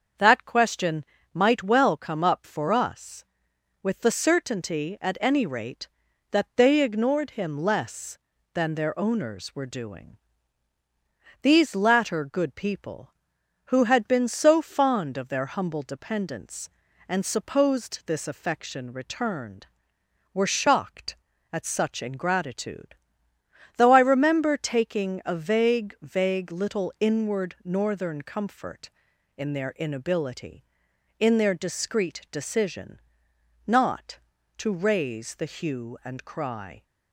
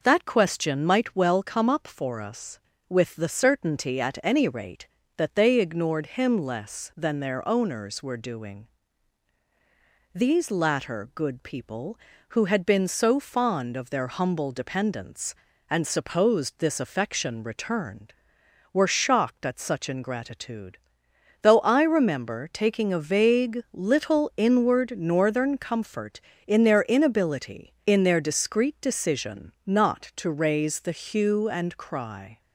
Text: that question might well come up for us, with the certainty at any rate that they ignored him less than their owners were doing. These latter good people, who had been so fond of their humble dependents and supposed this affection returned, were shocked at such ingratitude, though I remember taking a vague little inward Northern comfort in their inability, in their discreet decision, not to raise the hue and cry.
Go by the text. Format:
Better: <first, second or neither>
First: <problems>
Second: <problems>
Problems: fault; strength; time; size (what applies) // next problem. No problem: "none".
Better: second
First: starts louder than the rest; until 1.4 s; 7 dB // pauses between "question" and "might"; slight; at 1.0 s; 0.30 s long // says "vague" twice; at 26.0 s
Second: none